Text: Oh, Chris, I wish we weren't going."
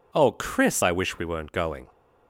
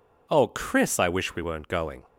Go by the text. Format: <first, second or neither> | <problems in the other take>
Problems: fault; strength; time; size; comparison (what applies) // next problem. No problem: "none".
neither | none